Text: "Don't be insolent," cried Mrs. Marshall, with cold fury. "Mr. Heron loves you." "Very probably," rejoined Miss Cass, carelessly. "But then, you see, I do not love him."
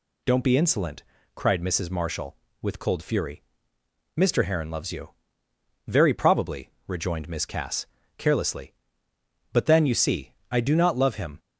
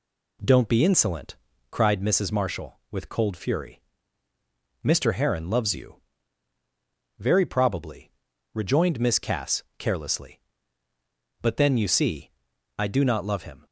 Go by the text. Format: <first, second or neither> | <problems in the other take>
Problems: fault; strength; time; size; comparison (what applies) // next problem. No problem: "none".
neither | none